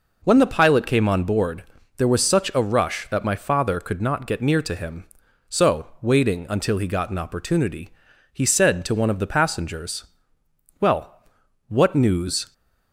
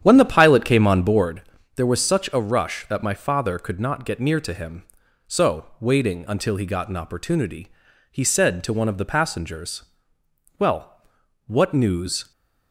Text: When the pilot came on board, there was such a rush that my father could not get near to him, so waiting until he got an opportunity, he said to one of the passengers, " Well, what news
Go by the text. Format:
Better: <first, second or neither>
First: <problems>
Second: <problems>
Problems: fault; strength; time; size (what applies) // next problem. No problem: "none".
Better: first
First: none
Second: starts louder than the rest; strong; until 1.4 s; 9.5 dB